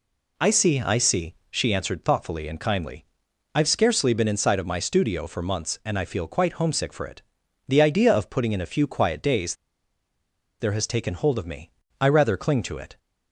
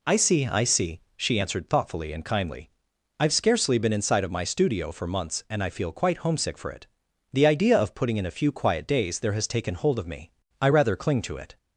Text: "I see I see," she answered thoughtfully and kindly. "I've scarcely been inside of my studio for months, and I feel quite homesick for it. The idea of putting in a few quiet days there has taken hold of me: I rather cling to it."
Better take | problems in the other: second | pauses between "days" and "there"; at 9.5 s; 1.0 s long

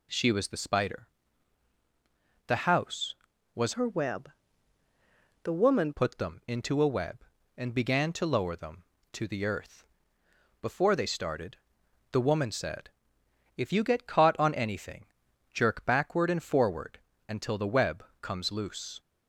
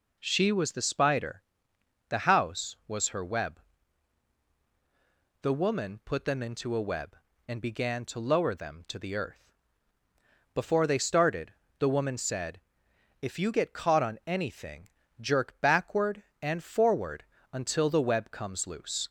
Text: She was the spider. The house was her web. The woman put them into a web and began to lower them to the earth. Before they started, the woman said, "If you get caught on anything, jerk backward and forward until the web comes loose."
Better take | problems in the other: second | changes voice from "her" to "woman"; from 3.7 to 5.9 s; 2.2 s long // pauses between "forward" and "until"; slight; at 16.9 s; 0.30 s long; slight in the second // pauses between "web" and "comes"; slight; at 18.0 s; 0.16 s long

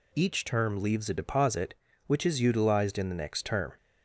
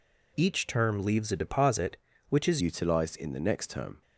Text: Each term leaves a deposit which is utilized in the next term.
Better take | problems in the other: first | changes voice at "utilized"; from 2.5 s on; 1.5 s long

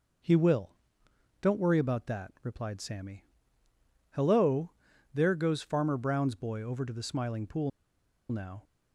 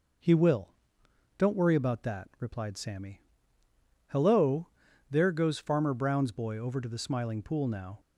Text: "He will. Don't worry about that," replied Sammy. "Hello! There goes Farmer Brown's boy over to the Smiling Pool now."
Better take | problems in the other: second | pauses between "Pool" and "now"; noticeable; at 7.7 s; 0.61 s long

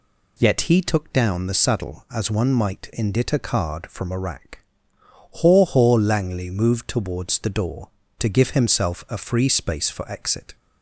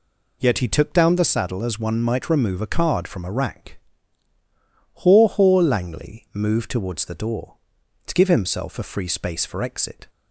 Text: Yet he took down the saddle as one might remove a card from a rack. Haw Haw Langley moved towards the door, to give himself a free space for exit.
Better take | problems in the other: second | says "indit" for "remove"; at 2.9 s

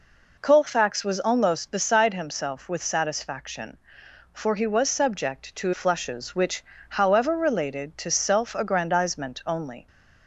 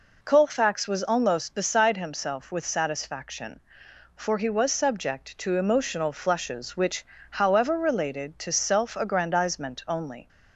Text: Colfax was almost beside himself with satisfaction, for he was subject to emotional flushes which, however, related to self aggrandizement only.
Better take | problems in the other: second | skips "emotional"; at 5.7 s

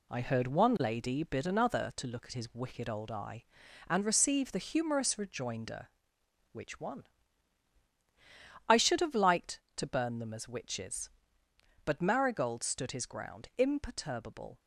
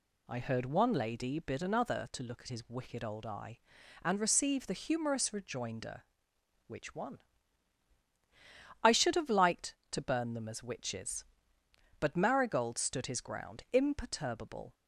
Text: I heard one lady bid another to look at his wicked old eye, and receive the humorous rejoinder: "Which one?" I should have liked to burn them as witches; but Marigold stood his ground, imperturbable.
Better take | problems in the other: second | gets quieter; noticeable; throughout; 6 dB

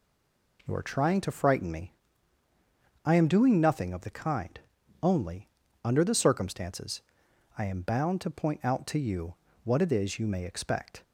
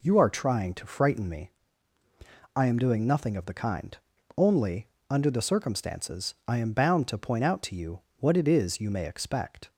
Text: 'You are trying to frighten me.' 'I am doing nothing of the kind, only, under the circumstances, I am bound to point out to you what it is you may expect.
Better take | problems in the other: second | stays silent before the first word; slight; until 0.5 s; 0.5 s long // pauses between "you" and "what"; slight; at 9.3 s; 0.30 s long; slight in the second

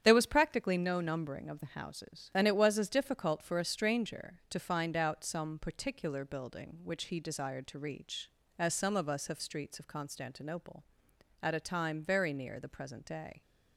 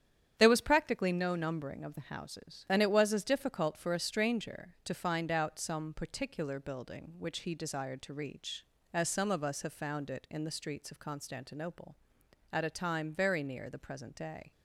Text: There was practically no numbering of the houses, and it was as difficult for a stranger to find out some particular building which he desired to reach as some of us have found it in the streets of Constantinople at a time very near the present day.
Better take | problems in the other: second | starts louder than the rest; strong; until 1.0 s; 9.5 dB; strong in the second // skips "found it in the"; at 9.3 s

